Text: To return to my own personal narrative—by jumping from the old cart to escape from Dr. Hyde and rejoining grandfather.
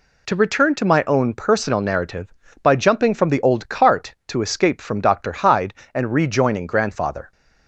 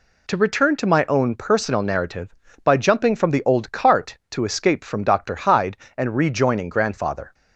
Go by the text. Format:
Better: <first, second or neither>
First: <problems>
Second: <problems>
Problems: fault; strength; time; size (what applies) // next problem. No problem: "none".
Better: neither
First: none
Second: none